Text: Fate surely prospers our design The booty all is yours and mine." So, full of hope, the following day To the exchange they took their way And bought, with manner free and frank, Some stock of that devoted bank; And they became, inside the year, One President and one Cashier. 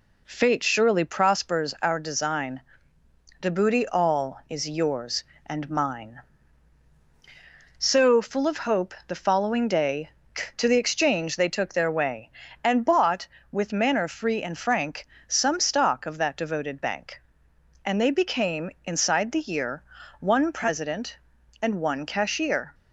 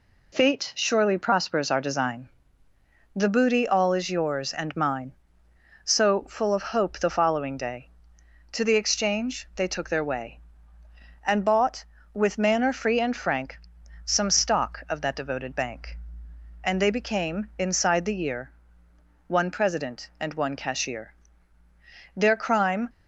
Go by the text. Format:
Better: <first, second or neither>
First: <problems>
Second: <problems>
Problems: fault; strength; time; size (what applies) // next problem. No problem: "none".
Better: first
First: pauses between "design" and "The"; noticeable; at 2.6 s; 0.80 s long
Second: pauses between "design" and "The"; noticeable; at 2.2 s; 0.88 s long // goes on to say "Their crime"; noticeable; from 22.1 s on; 0.74 s long